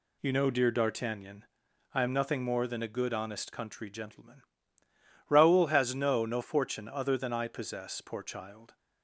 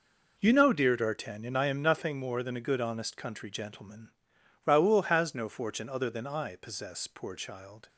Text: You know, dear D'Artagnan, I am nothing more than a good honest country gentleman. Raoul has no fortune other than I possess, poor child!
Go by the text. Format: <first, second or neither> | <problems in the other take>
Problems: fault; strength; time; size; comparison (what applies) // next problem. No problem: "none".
second | says "no" twice; at 6.2 s